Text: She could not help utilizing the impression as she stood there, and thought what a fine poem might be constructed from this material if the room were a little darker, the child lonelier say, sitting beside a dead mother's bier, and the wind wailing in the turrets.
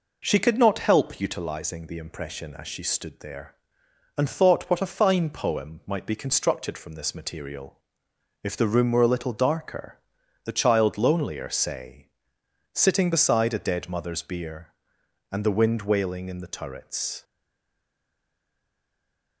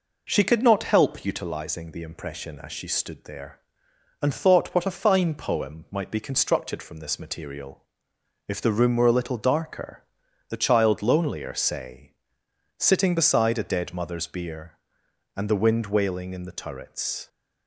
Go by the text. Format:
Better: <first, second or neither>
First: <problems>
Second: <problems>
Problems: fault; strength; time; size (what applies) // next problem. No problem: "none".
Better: second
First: pauses between "material" and "if"; noticeable; at 7.7 s; 0.64 s long // stays silent after the last word; from 17.2 s on; 2.2 s long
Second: pauses between "material" and "if"; noticeable; at 7.8 s; 0.64 s long